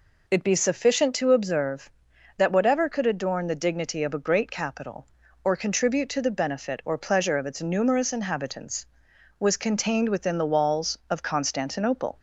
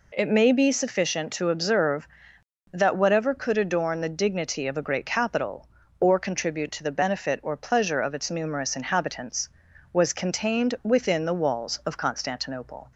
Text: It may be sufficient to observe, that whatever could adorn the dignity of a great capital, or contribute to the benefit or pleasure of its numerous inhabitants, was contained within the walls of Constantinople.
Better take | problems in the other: second | skips "may"; at 0.4 s

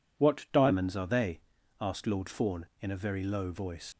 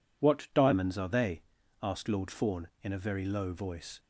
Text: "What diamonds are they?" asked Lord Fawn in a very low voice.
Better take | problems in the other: second | leaves "voice" unfinished; at 3.9 s; 55 ms

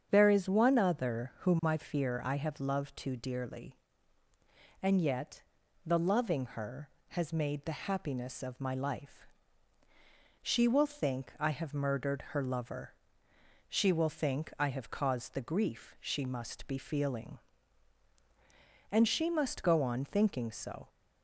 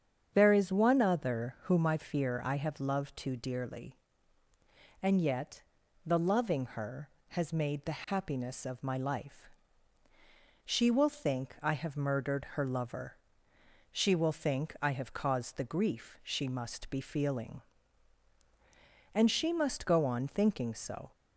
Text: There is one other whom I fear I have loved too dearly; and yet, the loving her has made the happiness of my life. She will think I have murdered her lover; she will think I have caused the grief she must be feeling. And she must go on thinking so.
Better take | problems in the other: neither | starts louder than the rest; strong; the same in both

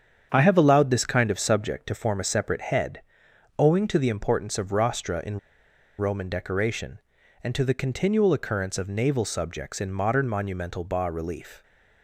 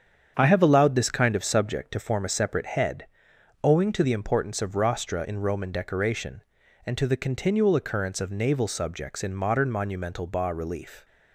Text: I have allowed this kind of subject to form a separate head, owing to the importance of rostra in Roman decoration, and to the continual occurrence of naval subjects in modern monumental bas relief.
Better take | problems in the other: second | starts louder than the rest; strong; until 1.3 s; 8 dB; strong in the second // pauses between "in" and "Roman"; noticeable; at 5.3 s; 0.61 s long

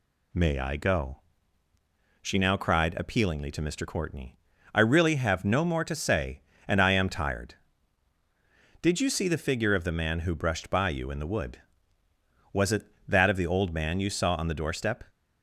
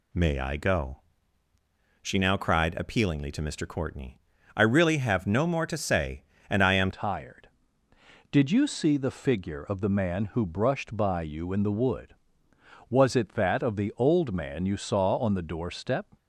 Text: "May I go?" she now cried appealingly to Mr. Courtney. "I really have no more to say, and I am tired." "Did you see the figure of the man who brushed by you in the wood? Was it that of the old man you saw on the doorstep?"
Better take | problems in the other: first | changes voice at "tired"; from 6.9 s on; 9.2 s long

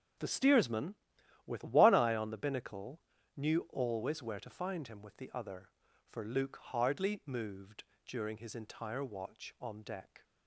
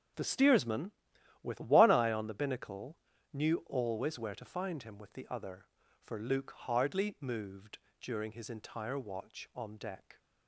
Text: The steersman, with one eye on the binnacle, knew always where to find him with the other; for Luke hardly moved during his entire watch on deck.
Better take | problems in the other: neither | starts louder than the rest; the same in both // pauses between "moved" and "during"; slight; the same in both

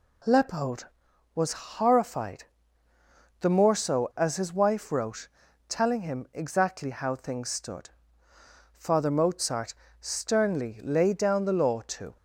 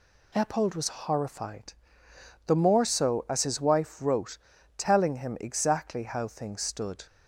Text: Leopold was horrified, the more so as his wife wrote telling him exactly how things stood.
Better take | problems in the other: second | pauses between "wrote" and "telling"; at 5.2 s; 0.40 s long; also in the second // goes on to say "Father Mozart sternly laid down the law to"; strong; from 8.7 s on; 3.4 s long

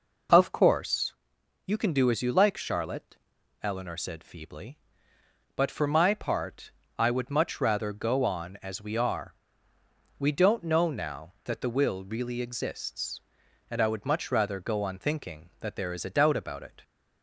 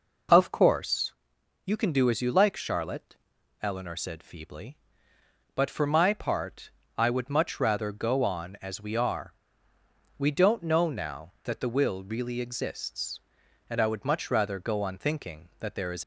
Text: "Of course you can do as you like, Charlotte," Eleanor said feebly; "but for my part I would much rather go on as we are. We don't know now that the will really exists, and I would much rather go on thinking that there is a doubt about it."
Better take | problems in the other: first | pauses between "course" and "you"; noticeable; at 1.1 s; 0.52 s long; noticeable in the first // pauses between "part" and "I"; slight; at 6.6 s; 0.26 s long; slight in the first // stops before "a doubt about it"; at 16.0 s

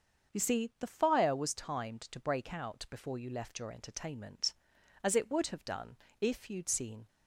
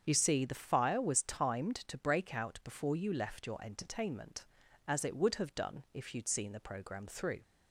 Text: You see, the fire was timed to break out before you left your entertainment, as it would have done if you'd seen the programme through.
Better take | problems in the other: second | starts louder than the rest; until 1.3 s; 6.5 dB; strong in the second // pauses between "done" and "if"; slight; at 5.9 s; 0.24 s long // stops before "the programme through"; at 7.0 s

